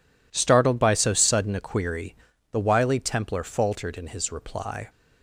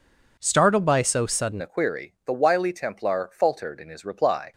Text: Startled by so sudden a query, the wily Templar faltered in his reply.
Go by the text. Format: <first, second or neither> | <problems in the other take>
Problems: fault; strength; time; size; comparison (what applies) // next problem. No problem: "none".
first | changes voice at "a"; from 1.6 s on; 2.9 s long